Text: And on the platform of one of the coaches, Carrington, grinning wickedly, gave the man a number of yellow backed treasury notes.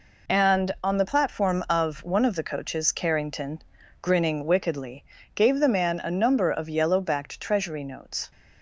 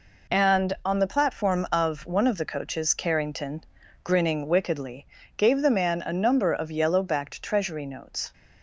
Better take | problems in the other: neither | none

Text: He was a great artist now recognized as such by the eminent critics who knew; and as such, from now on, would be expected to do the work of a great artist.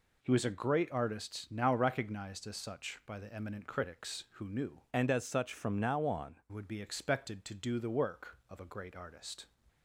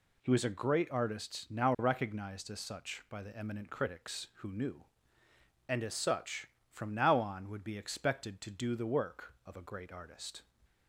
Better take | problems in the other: second | changes voice from "and" to "on"; from 4.9 to 6.4 s; 1.5 s long

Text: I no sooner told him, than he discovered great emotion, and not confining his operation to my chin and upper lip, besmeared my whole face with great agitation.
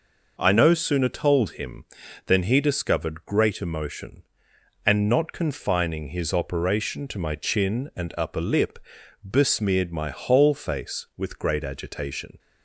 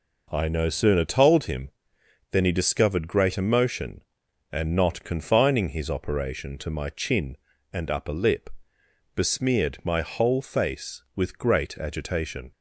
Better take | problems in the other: neither | none

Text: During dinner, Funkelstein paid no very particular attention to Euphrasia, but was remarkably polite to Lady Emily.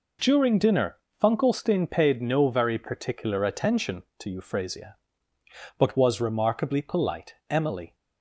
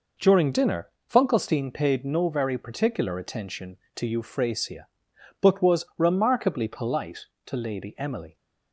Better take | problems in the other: second | skips "to Lady"; at 7.4 s

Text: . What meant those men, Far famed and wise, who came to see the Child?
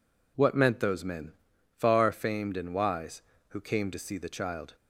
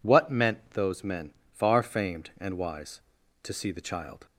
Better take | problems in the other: first | skips "who came"; at 3.2 s

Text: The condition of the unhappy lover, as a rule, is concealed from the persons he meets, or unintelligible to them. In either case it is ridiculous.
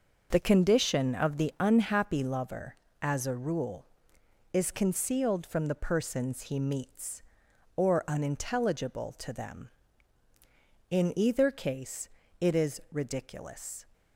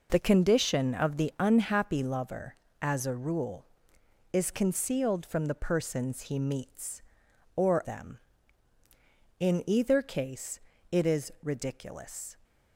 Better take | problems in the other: first | skips "unintelligible to"; at 7.8 s // pauses between "case" and "it"; slight; at 10.6 s; 0.30 s long; slight in the first

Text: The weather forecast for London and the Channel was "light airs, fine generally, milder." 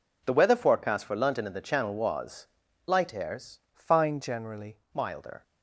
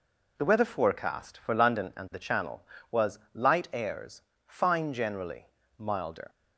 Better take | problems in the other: second | pauses between "was" and "light"; at 2.4 s; 0.40 s long; slight in the second // changes voice from "fine" to "generally"; from 3.7 to 4.7 s; 1.0 s long

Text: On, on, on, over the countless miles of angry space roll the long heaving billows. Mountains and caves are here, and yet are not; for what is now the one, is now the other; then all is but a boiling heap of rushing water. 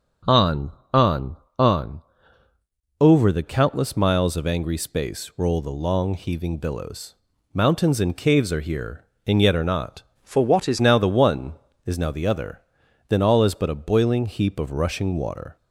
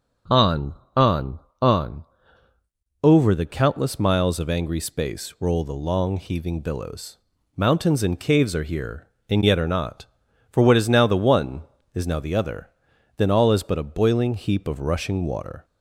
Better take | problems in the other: second | starts louder than the rest; until 1.7 s; 6.5 dB; also in the second // changes voice from "for" to "is"; from 10.2 to 10.8 s; 0.6 s long

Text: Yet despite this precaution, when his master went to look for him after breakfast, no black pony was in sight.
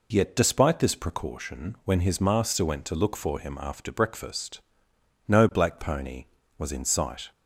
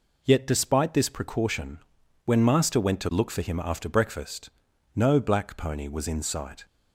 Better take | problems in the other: first | skips "his"; at 2.4 s

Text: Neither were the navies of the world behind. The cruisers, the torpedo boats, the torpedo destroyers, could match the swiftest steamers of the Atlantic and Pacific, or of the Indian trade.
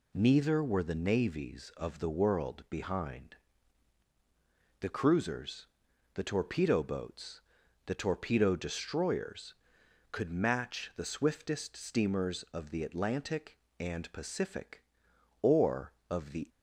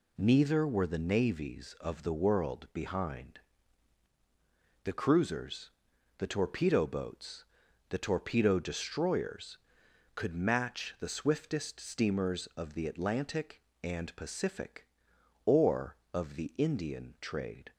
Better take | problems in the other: second | stops before "Indian trade"; at 16.4 s

